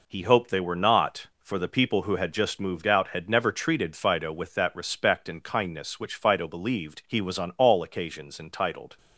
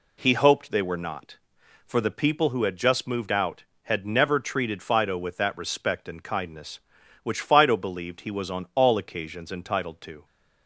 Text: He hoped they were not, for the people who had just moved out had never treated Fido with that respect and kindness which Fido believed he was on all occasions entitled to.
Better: second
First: stops before "to"; at 8.9 s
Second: none

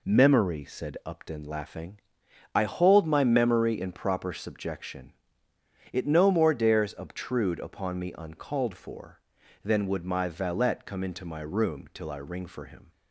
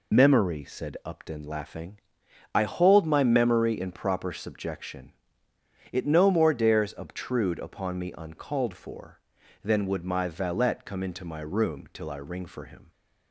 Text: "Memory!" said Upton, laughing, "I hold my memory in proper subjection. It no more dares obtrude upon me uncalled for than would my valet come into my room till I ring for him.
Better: first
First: none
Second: loses the start of "Memory"; at 0.1 s; 70 ms

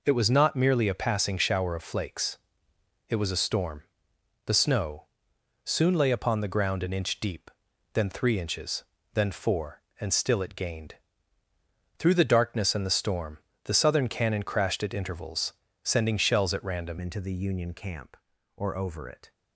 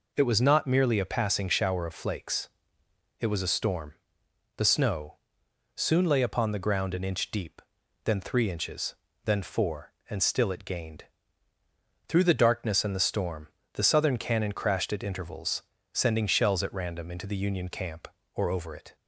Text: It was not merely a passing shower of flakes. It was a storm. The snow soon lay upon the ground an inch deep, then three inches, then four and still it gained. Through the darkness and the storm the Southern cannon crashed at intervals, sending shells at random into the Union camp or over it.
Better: second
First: pauses between "snow" and "soon"; noticeable; at 5.0 s; 0.58 s long // pauses between "storm" and "the"; slight; at 13.3 s; 0.28 s long // changes voice at "into"; from 17.0 s on; 2.3 s long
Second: pauses between "snow" and "soon"; noticeable; at 5.1 s; 0.58 s long // pauses between "storm" and "the"; slight; at 13.4 s; 0.28 s long

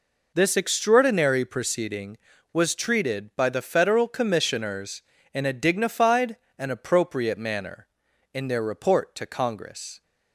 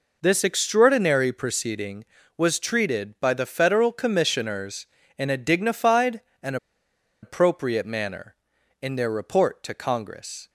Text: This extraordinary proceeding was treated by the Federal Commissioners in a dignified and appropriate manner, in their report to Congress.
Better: first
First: none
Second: pauses between "and" and "appropriate"; noticeable; at 6.5 s; 0.66 s long

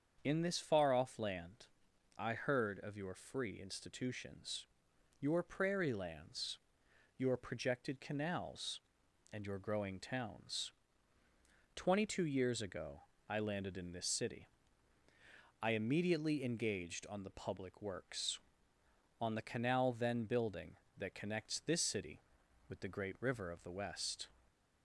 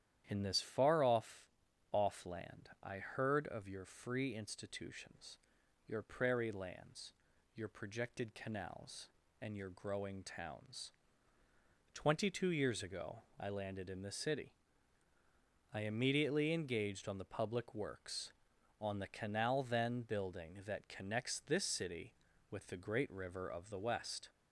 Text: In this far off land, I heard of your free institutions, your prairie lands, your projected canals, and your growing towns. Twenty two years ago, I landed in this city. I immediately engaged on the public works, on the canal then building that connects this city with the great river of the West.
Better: first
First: starts louder than the rest; until 1.2 s; 7 dB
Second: starts louder than the rest; strong; until 1.2 s; 10.5 dB // says "off" twice; at 1.9 s

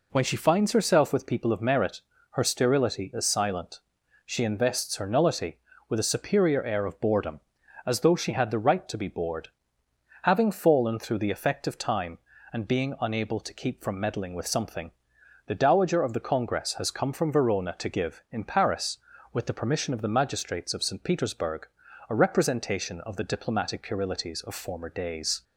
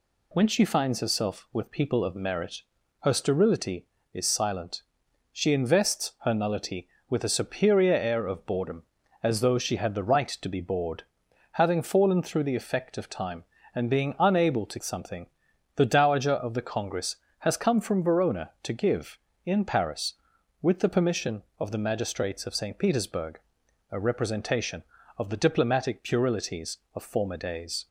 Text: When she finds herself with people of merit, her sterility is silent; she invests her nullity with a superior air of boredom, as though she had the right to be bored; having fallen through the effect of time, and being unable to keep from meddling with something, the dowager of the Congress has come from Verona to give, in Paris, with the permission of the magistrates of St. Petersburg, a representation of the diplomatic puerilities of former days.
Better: first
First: none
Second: skips "keep from meddling with"; at 14.8 s

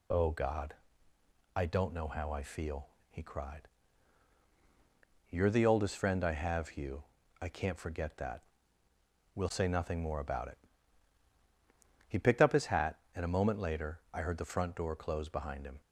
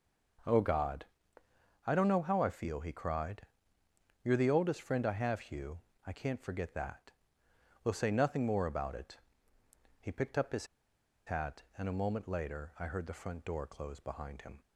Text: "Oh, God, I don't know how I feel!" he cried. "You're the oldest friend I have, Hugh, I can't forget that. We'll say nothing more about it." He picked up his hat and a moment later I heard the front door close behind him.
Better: first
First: none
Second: pauses between "his" and "hat"; noticeable; at 10.6 s; 0.60 s long

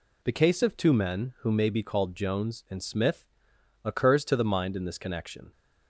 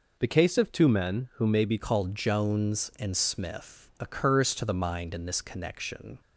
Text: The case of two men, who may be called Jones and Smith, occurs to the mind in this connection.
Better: first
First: none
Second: changes voice at "called"; from 1.7 s on; 4.4 s long

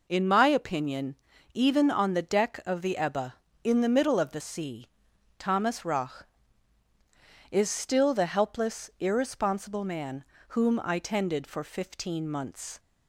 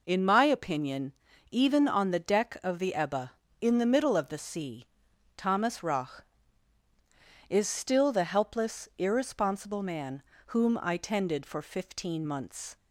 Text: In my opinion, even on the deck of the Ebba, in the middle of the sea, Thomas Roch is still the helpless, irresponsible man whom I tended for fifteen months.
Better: neither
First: pauses between "man" and "whom"; slight; at 10.2 s; 0.26 s long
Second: pauses between "man" and "whom"; slight; at 10.2 s; 0.26 s long

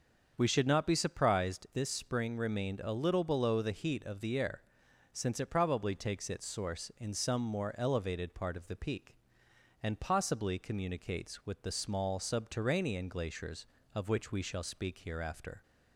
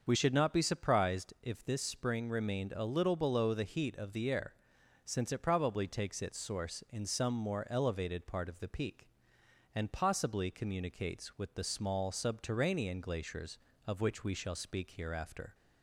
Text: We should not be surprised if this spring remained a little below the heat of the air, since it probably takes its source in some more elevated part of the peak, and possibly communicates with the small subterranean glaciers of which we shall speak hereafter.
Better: second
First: starts louder than the rest; until 1.3 s; 6.5 dB // skips "if"; at 1.6 s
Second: starts louder than the rest; until 1.0 s; 6.5 dB

